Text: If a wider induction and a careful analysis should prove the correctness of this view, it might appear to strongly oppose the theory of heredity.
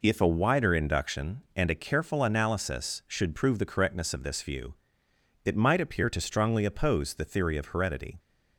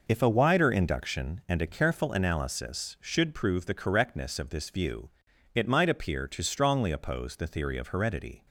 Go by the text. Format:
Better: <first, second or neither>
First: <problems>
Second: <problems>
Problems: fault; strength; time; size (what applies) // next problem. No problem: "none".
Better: neither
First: none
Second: none